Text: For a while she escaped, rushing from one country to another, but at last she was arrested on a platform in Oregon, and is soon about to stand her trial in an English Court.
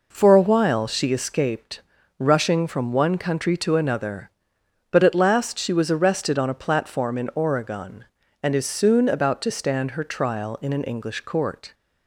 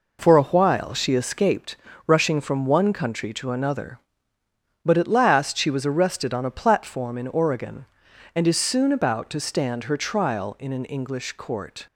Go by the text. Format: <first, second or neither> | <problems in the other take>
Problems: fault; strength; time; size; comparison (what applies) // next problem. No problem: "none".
neither | none